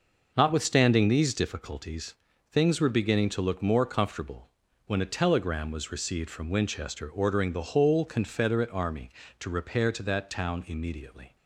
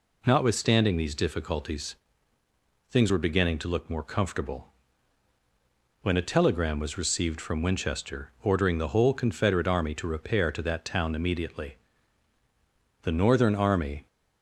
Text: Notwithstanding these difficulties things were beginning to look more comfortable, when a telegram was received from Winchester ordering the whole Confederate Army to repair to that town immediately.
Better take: first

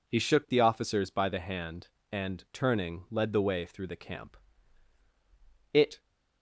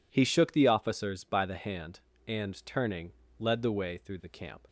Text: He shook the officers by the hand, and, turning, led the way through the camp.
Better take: second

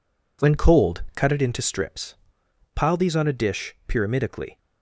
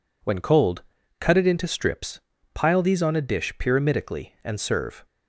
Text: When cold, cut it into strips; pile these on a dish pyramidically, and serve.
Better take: second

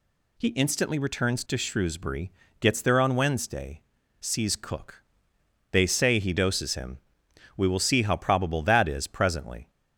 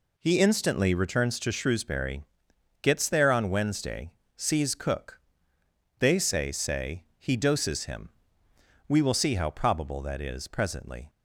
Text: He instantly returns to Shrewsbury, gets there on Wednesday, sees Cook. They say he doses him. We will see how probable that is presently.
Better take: first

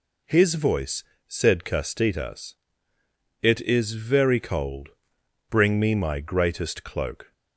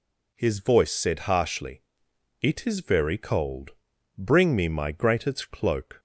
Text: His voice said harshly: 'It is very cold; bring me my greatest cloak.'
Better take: second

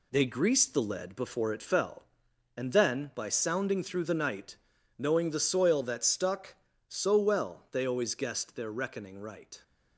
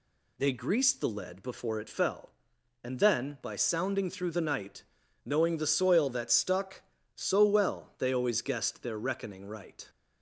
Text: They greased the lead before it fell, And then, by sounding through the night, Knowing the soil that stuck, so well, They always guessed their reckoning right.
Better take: second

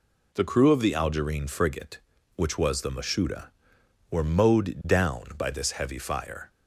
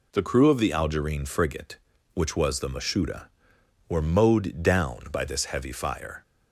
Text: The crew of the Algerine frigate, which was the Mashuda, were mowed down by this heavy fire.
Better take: neither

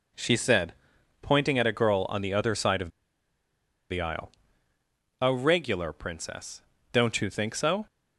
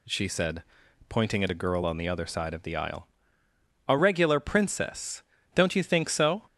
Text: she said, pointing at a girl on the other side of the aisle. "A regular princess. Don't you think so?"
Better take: second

